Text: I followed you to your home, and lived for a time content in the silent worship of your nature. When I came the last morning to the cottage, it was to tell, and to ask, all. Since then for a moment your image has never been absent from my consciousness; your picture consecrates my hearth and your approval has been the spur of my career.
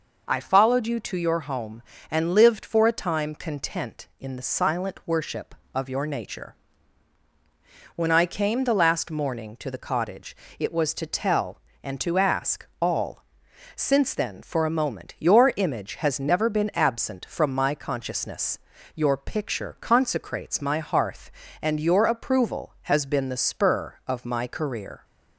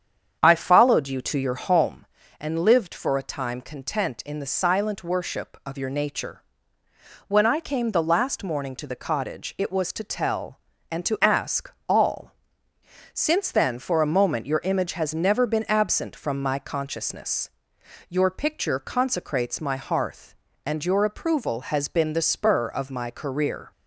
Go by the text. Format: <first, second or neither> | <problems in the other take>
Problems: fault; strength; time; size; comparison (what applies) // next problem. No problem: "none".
first | starts louder than the rest; strong; until 1.9 s; 8 dB